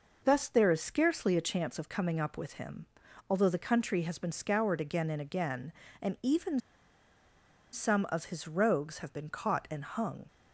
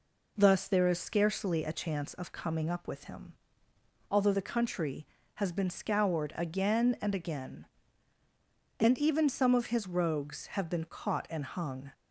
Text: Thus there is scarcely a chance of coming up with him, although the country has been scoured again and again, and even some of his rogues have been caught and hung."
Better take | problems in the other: second | pauses between "even" and "some"; at 6.5 s; 1.1 s long

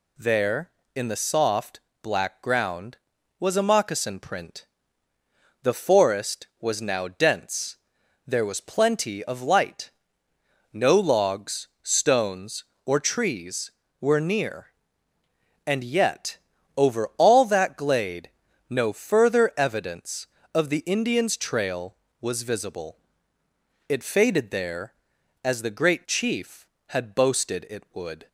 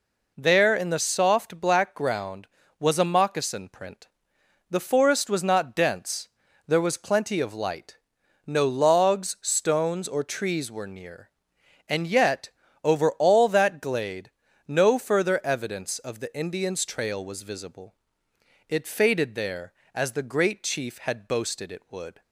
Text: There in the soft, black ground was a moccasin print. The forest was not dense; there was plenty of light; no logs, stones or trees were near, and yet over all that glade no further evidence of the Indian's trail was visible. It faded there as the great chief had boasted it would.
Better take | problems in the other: second | says "now" for "not"; at 6.8 s // pauses between "yet" and "over"; at 16.3 s; 0.38 s long; slight in the second // pauses between "glade" and "no"; at 18.2 s; 0.40 s long; slight in the second

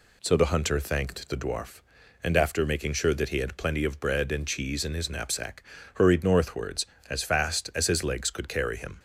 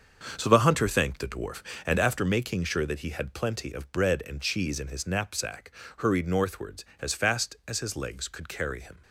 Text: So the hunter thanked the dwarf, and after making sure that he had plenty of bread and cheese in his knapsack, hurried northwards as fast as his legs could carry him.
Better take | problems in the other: first | gets quieter; strong; throughout; 8.5 dB

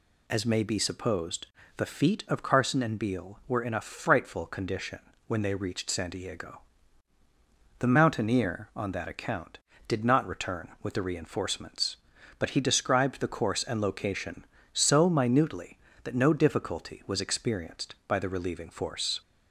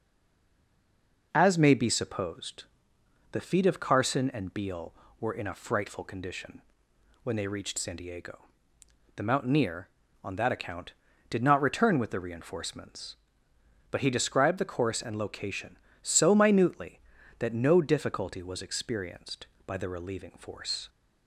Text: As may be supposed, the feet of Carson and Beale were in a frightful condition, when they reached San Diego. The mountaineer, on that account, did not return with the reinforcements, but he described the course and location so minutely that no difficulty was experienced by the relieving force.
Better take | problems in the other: first | stays silent before the first word; noticeable; until 1.3 s; 1.3 s long

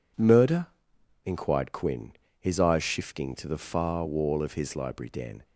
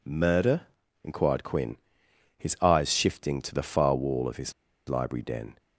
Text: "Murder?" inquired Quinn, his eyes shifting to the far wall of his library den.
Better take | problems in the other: first | pauses between "his" and "library"; at 4.5 s; 0.36 s long

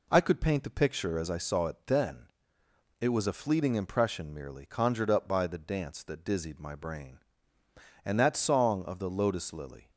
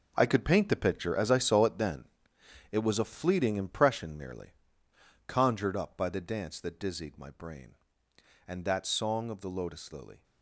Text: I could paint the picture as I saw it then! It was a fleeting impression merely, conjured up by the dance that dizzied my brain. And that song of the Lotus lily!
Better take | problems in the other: first | gets quieter; strong; throughout; 11.5 dB

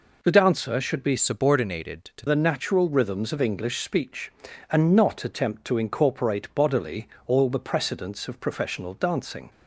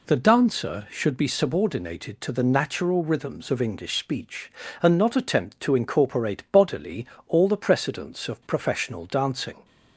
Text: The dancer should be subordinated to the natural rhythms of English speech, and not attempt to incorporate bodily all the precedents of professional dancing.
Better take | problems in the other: second | changes voice from "subordinated" to "to"; from 1.1 to 2.2 s; 1.1 s long // pauses between "bodily" and "all"; slight; at 7.0 s; 0.22 s long; slight in the second

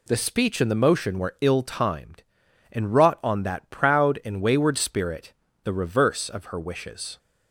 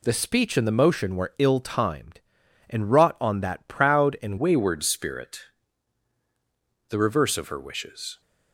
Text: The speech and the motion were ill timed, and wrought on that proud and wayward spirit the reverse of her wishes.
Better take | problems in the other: first | changes voice at "wayward"; from 4.3 s on; 3.9 s long // pauses between "spirit" and "the"; strong; at 5.4 s; 1.4 s long; slight in the first

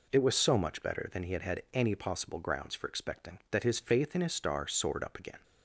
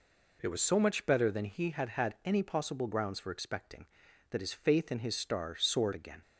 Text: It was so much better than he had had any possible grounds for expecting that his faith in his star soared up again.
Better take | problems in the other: first | skips "up"; at 5.9 s

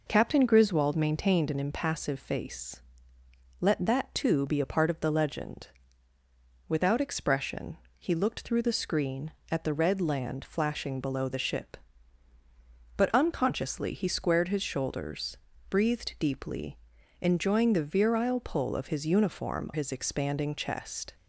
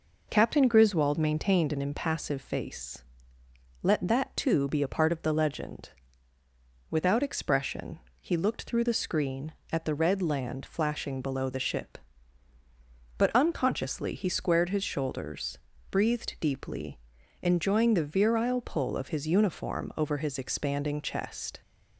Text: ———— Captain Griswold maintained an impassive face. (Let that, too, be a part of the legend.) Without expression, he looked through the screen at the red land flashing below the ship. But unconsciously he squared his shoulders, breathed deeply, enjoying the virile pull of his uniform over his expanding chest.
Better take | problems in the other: second | skips "over"; at 19.7 s

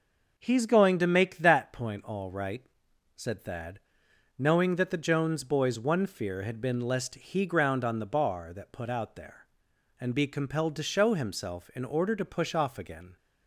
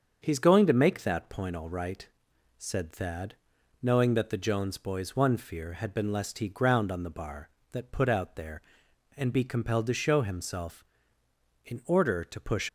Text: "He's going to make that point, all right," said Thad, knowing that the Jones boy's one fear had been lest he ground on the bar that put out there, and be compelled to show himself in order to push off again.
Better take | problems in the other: first | starts louder than the rest; until 1.2 s; 7 dB // stops before "off again"; at 12.6 s

